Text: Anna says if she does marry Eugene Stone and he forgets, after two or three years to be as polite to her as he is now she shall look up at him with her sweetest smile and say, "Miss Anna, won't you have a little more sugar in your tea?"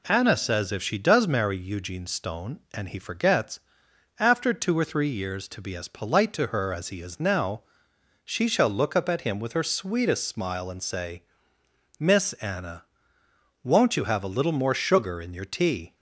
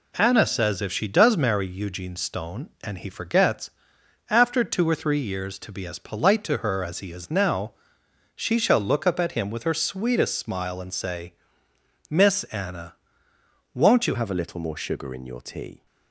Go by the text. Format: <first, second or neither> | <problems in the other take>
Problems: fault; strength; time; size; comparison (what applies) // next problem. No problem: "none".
first | pauses between "now" and "she"; noticeable; at 7.7 s; 0.62 s long; noticeable in the first // changes voice at "have"; from 14.1 s on; 1.7 s long